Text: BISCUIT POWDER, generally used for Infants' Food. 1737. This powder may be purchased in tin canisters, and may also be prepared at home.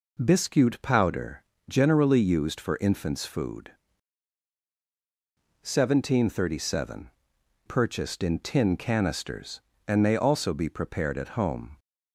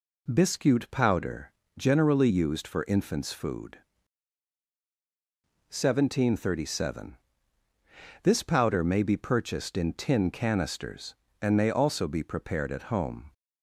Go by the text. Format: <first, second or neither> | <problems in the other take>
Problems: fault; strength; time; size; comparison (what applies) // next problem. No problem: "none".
second | skips "This powder may be"; at 7.3 s